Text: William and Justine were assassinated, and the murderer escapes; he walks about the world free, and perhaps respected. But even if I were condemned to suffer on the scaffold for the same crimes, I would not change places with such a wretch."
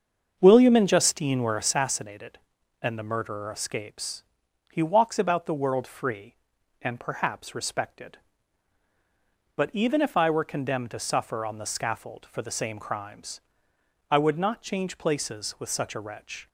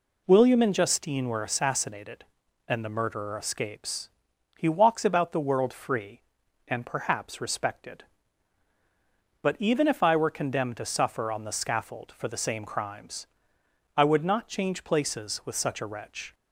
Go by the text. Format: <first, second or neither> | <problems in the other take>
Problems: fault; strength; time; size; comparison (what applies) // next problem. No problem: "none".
second | starts louder than the rest; until 1.8 s; 6.5 dB